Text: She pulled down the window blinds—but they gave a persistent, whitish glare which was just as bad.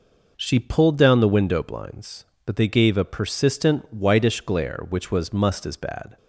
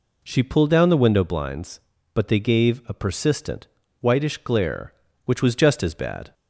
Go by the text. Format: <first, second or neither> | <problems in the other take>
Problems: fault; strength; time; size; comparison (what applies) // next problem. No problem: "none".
second | says "must" for "just"; at 5.3 s